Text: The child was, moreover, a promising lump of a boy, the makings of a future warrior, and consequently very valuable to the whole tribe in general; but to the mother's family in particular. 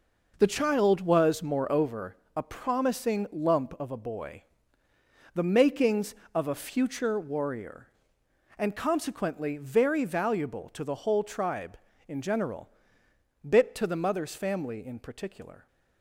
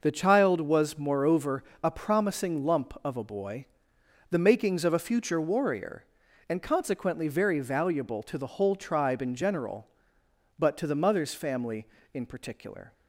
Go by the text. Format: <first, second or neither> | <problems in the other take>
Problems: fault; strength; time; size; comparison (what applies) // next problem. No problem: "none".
second | says "bit" for "but"; at 13.4 s